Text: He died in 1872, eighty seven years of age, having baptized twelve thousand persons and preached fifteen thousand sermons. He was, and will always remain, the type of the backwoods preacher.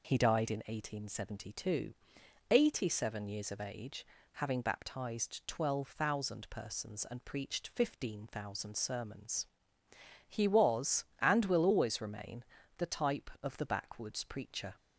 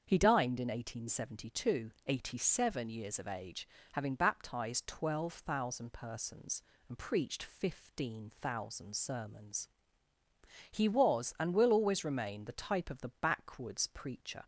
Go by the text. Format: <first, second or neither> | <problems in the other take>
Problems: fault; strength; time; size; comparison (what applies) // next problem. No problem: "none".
first | starts louder than the rest; until 1.0 s; 7 dB // says "dined" for "died"; at 0.1 s